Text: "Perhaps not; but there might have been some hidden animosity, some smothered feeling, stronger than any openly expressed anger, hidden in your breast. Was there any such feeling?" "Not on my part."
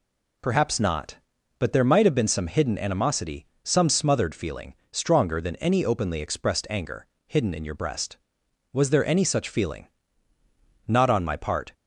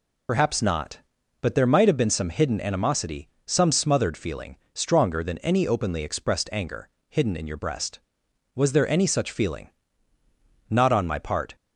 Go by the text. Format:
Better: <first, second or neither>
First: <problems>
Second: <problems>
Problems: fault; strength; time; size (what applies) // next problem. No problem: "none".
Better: first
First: none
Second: loses the start of "Perhaps"; at 0.2 s; 60 ms